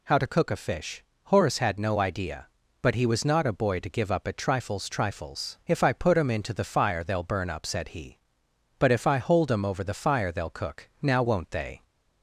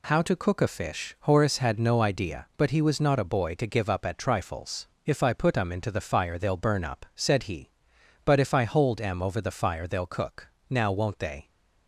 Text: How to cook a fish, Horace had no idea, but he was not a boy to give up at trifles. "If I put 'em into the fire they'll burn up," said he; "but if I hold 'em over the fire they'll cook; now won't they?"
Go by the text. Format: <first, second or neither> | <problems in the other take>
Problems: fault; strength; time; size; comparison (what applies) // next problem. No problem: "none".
second | says "trifles" twice; at 4.8 s